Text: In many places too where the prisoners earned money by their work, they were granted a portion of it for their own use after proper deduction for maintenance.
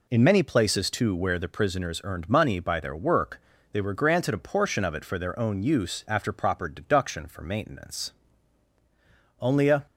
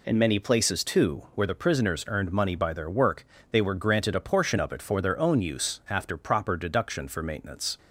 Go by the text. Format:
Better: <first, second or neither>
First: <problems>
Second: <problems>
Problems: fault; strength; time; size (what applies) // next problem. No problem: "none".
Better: second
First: goes on to say "Only a"; slight; from 9.3 s on; 0.46 s long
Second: none